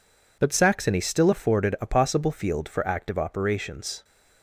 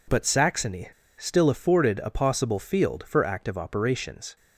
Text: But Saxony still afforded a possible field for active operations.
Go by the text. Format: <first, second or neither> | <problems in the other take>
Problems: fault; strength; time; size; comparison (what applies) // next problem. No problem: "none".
first | pauses between "Saxony" and "still"; slight; at 0.8 s; 0.30 s long